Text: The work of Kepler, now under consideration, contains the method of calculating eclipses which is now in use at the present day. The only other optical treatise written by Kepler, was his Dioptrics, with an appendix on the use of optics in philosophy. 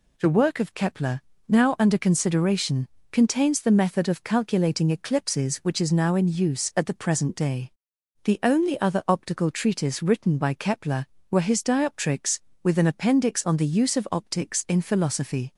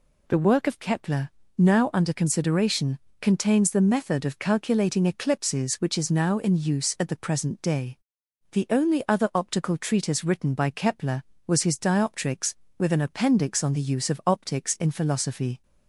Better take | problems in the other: second | says "were" for "was"; at 11.3 s

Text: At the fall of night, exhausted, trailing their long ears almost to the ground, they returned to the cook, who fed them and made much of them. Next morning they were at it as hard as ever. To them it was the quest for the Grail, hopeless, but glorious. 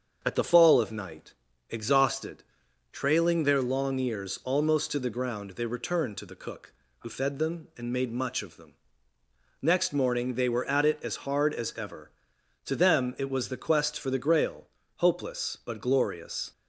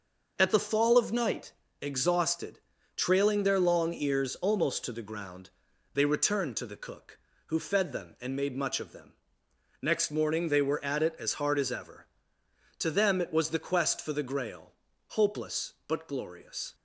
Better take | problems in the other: neither | starts louder than the rest; the same in both

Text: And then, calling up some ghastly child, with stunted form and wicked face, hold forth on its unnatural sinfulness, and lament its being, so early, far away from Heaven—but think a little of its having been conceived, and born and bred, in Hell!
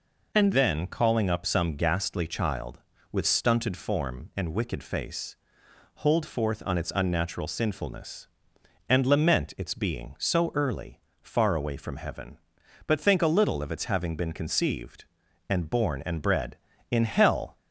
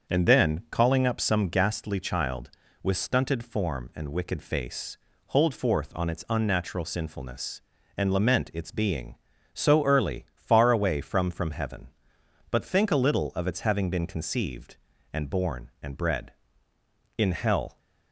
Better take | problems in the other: first | starts louder than the rest; until 1.1 s; 6.5 dB // says "from" twice; at 11.2 s

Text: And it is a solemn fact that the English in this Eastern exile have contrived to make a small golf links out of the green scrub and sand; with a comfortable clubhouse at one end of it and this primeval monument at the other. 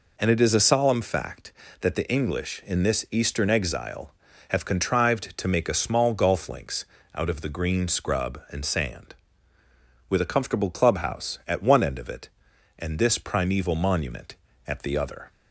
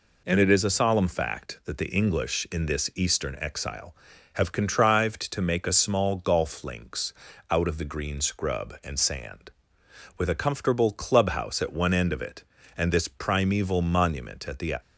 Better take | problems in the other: first | pauses between "links" and "out"; at 7.1 s; 0.38 s long; slight in the first // stops before "other"; at 14.8 s

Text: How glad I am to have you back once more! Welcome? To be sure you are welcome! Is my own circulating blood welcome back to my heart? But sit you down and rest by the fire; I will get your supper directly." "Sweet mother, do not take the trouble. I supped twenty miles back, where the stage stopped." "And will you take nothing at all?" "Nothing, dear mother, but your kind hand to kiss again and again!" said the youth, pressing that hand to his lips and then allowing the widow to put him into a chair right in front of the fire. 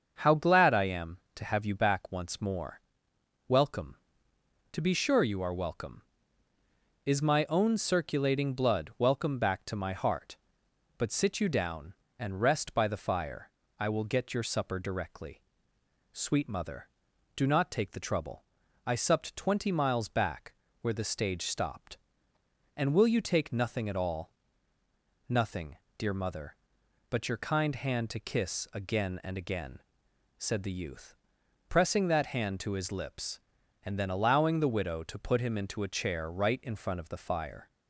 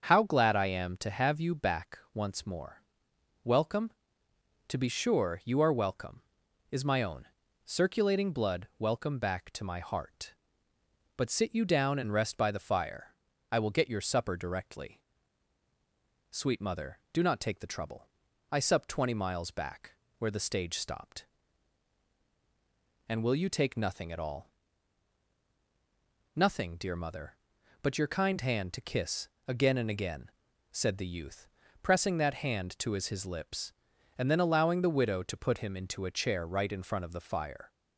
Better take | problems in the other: first | starts louder than the rest; until 1.0 s; 7 dB; also in the first // pauses between "back" and "once"; slight; at 1.9 s; 0.16 s long // pauses between "own" and "circulating"; at 7.2 s; 0.40 s long // pauses between "kiss" and "again"; slight; at 29.2 s; 0.16 s long // says "his" twice; at 33.0 s

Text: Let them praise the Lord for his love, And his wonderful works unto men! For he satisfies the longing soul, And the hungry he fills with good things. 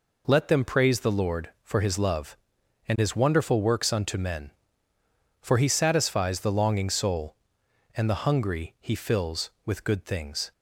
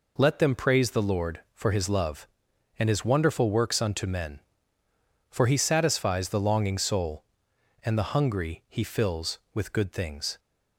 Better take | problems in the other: neither | none

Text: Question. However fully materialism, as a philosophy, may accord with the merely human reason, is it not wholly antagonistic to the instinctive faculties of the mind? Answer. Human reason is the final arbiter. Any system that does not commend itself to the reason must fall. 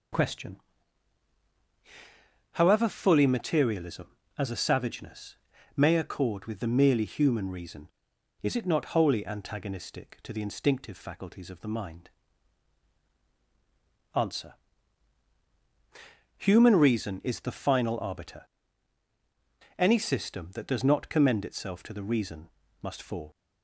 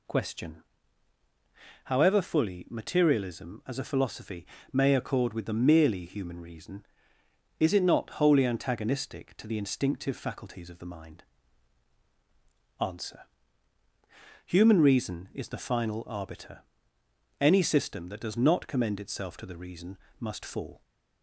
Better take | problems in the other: second | says "savageness" for "philosophy"; at 4.5 s // pauses between "reason" and "must"; slight; at 22.4 s; 0.34 s long; slight in the second

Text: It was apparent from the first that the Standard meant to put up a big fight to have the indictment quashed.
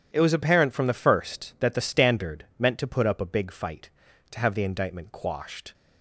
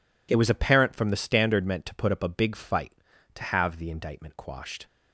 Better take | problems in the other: first | skips "first that the"; at 1.1 s

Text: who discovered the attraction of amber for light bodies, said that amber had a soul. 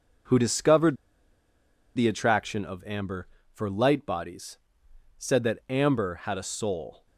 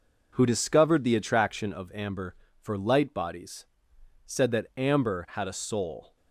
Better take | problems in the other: second | pauses between "discovered" and "the"; at 0.9 s; 0.99 s long

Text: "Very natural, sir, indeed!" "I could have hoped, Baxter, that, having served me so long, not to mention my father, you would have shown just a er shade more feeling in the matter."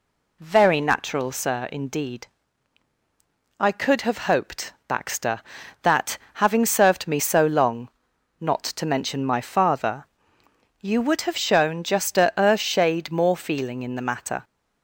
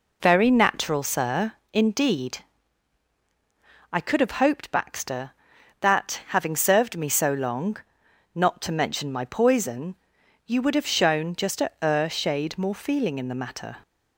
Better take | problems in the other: first | says "poison" for "father"; at 9.2 s

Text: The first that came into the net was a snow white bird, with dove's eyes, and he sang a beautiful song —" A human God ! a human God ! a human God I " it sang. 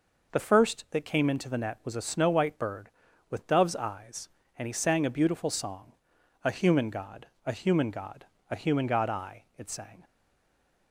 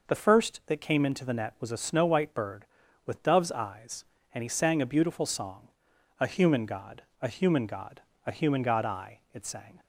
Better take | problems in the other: second | stays silent after the last word; slight; from 10.0 s on; 0.9 s long

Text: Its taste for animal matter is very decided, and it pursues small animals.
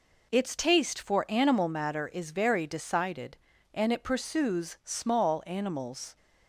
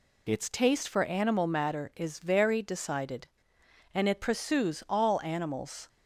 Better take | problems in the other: first | says "all" for "small"; at 4.8 s

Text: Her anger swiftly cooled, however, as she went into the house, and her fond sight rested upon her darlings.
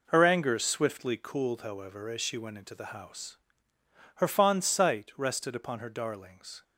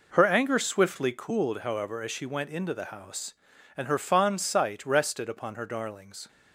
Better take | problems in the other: second | skips "and"; at 3.7 s

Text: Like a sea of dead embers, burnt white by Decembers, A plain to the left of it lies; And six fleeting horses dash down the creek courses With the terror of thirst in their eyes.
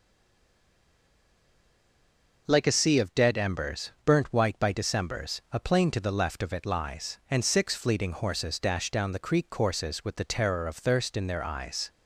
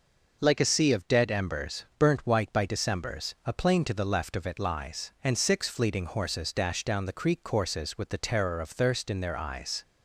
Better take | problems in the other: second | stays silent before the first word; until 2.4 s; 2.4 s long

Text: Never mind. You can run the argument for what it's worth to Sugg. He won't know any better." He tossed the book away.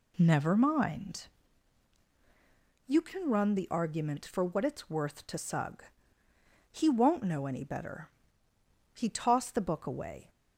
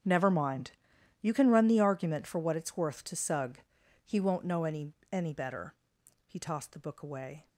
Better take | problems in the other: first | starts louder than the rest; strong; until 1.5 s; 8 dB // says "any" twice; at 5.1 s

